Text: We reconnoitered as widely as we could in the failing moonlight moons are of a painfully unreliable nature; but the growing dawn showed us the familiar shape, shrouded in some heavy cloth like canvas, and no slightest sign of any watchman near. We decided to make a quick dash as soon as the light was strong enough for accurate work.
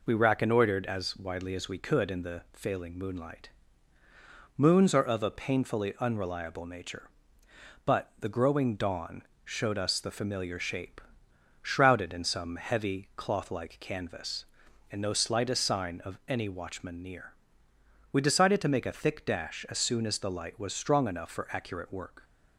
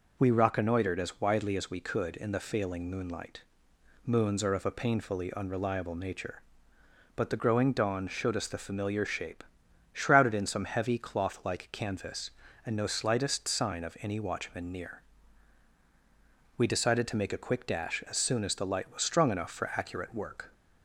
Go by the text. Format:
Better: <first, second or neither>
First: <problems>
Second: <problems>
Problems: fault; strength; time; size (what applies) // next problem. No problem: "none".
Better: second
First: pauses between "moonlight" and "moons"; at 3.4 s; 1.0 s long // pauses between "dawn" and "showed"; slight; at 9.2 s; 0.22 s long // says "thick" for "quick"; at 18.9 s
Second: pauses between "moonlight" and "moons"; noticeable; at 3.4 s; 0.64 s long